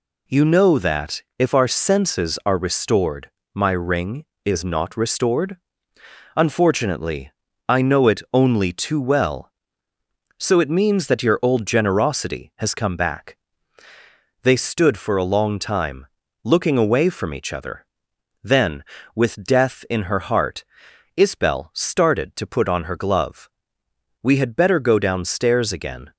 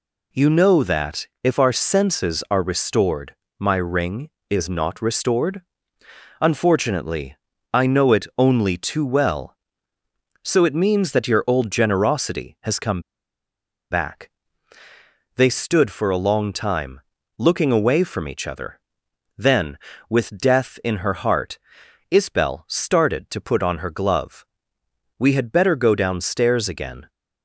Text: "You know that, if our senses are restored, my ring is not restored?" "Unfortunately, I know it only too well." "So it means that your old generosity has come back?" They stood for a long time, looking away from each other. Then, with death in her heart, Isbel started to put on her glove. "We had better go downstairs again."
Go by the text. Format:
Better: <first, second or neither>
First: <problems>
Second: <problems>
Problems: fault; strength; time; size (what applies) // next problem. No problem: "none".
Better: first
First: none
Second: pauses between "come" and "back"; noticeable; at 13.0 s; 0.89 s long